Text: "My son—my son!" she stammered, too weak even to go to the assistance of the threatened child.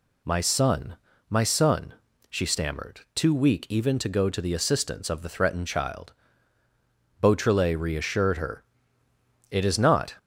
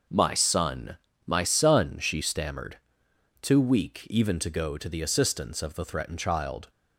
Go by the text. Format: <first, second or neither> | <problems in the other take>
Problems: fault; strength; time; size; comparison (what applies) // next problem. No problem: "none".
second | goes on to say "Beautrelet reassured her It is not"; strong; from 7.2 s on; 2.9 s long